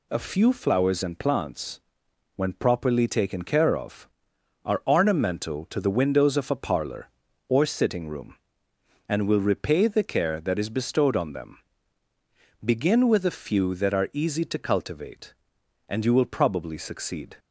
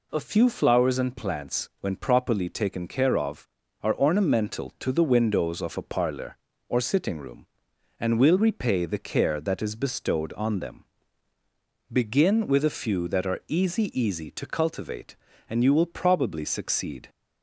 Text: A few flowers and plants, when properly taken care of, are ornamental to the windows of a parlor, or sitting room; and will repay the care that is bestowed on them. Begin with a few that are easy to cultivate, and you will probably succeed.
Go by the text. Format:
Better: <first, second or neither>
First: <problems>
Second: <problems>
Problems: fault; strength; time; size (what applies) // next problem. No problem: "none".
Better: first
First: none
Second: says "easy" twice; at 14.0 s